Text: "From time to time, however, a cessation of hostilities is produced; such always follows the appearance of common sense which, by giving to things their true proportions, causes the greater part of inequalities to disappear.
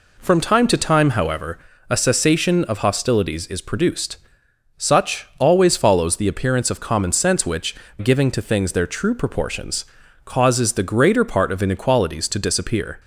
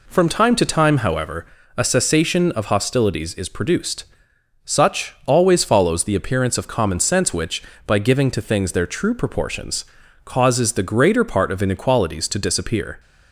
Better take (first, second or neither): second